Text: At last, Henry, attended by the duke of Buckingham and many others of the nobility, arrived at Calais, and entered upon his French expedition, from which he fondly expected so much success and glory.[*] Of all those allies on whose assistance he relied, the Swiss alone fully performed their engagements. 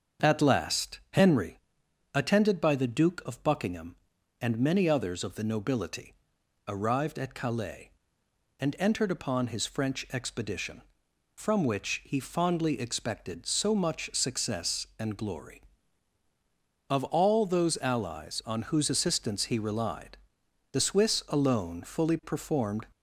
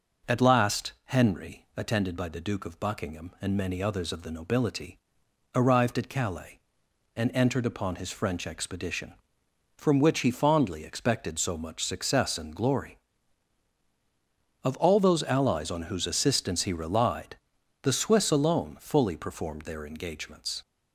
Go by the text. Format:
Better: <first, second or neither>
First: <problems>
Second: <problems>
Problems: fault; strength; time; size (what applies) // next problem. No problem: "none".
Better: second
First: starts louder than the rest; until 1.3 s; 7 dB // stops before "their engagements"; at 22.9 s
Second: none